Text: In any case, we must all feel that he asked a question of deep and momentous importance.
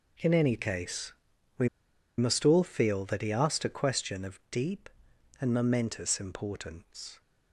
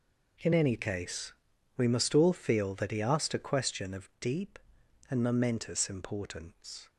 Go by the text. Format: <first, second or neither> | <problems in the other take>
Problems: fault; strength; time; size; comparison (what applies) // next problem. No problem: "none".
second | pauses between "we" and "must"; noticeable; at 1.6 s; 0.49 s long